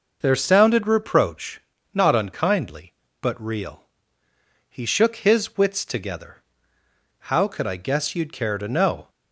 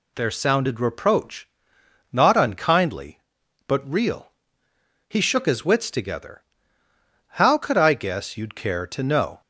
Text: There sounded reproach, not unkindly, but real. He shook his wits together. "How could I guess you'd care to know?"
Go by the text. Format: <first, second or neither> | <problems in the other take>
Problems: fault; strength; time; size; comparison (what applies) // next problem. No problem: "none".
neither | none